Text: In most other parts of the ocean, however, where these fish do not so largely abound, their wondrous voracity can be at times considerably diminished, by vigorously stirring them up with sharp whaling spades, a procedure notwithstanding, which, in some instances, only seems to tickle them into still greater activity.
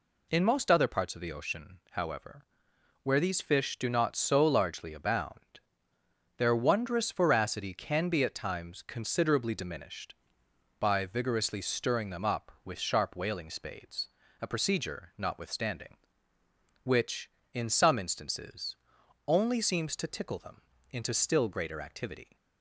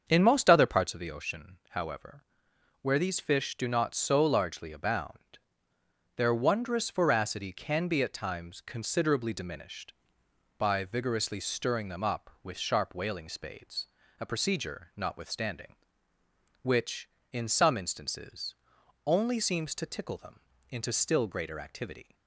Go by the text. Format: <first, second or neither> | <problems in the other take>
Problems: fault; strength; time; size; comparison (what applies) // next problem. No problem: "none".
first | starts louder than the rest; strong; until 1.0 s; 7 dB // pauses between "them" and "into"; slight; at 20.3 s; 0.30 s long; slight in the first